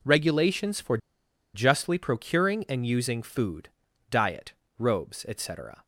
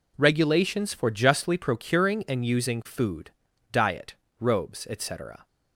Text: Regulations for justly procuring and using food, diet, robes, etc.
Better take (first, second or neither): second